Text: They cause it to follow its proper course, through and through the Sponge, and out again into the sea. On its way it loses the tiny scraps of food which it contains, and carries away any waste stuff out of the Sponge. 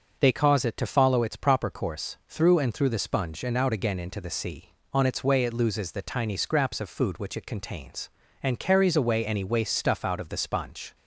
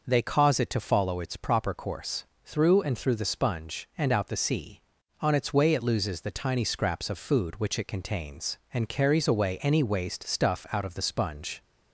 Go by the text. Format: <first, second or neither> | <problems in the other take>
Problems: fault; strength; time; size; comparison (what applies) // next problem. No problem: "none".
first | skips "again into"; at 4.2 s